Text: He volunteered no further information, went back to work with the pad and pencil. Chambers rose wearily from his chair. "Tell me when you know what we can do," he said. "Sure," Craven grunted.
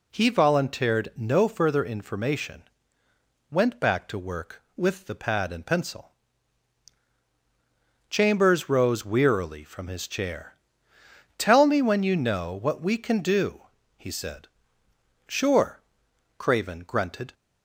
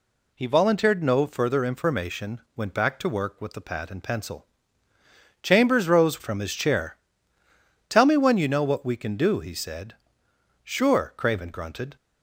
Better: first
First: none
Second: skips "wearily"; at 6.2 s

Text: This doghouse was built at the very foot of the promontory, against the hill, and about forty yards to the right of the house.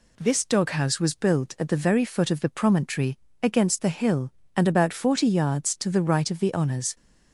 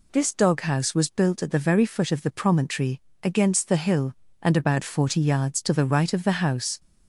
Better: second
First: says "honors" for "house"; at 6.5 s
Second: none

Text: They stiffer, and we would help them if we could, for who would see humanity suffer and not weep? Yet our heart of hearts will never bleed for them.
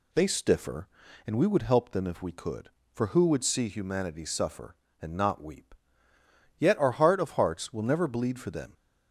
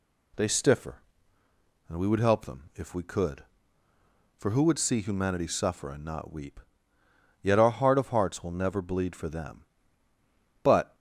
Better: first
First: none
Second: goes on to say "But"; slight; from 10.6 s on; 0.32 s long

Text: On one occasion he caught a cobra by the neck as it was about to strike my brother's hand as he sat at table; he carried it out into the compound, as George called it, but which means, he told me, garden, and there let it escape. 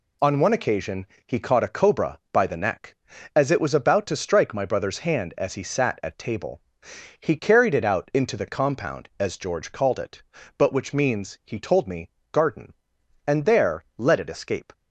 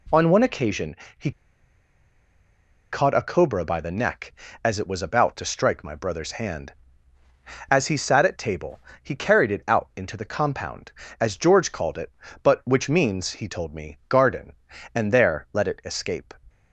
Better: first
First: pauses between "occasion" and "he"; slight; at 1.0 s; 0.18 s long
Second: pauses between "occasion" and "he"; slight; at 0.9 s; 0.22 s long // pauses between "he" and "caught"; strong; at 1.3 s; 1.6 s long

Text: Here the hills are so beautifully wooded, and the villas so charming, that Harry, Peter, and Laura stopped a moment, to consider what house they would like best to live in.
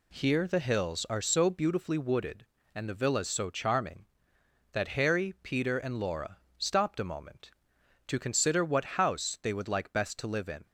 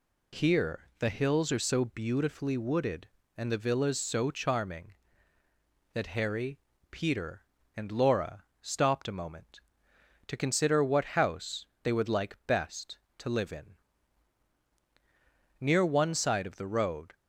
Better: first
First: pauses between "Laura" and "stopped"; slight; at 6.3 s; 0.22 s long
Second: pauses between "Laura" and "stopped"; slight; at 8.4 s; 0.18 s long // pauses between "house" and "they"; slight; at 11.6 s; 0.18 s long // goes on to say "Near one side of the road"; from 15.5 s on; 1.5 s long

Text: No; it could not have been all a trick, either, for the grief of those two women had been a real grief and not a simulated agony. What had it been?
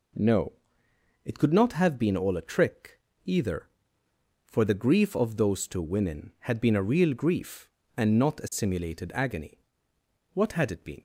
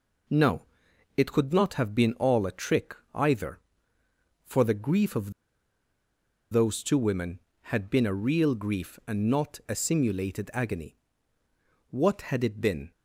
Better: first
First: none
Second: pauses between "of" and "those"; at 5.3 s; 1.2 s long

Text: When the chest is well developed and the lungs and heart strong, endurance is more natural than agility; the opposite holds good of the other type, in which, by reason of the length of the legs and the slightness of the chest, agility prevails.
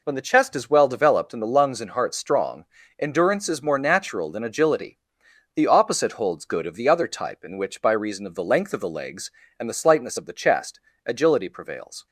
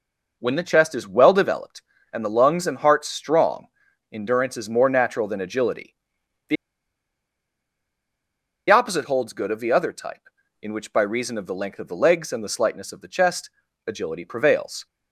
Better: first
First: none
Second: pauses between "the" and "opposite"; strong; at 6.5 s; 2.1 s long

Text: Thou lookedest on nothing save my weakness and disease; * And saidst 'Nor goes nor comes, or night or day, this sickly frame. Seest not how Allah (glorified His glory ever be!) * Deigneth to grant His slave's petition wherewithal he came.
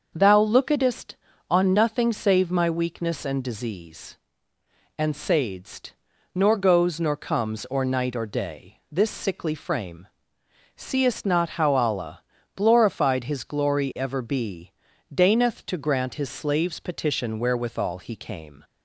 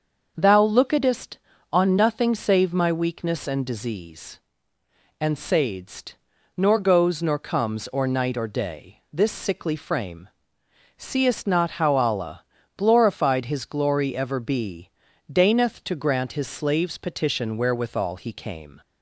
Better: neither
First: starts louder than the rest; until 1.1 s; 6.5 dB // pauses between "saidst" and "Nor"; at 5.9 s; 0.42 s long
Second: starts louder than the rest; until 1.3 s; 6.5 dB // pauses between "saidst" and "Nor"; at 6.1 s; 0.42 s long

